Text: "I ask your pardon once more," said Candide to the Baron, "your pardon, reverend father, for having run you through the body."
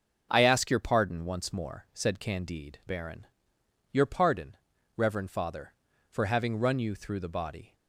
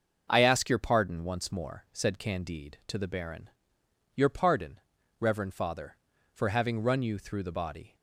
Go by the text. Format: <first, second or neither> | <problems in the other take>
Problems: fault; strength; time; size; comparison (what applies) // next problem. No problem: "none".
second | starts louder than the rest; until 1.3 s; 6.5 dB; noticeable in the second // skips "to the"; at 2.8 s